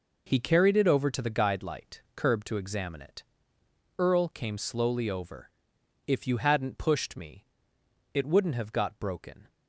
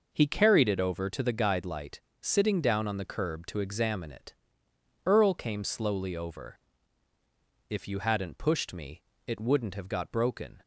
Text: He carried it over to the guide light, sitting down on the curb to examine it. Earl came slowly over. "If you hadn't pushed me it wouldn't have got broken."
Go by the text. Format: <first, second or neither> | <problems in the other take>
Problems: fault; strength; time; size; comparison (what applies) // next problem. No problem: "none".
second | skips "sitting down on the"; at 2.0 s // pauses between "me" and "it"; noticeable; at 7.4 s; 0.70 s long; slight in the second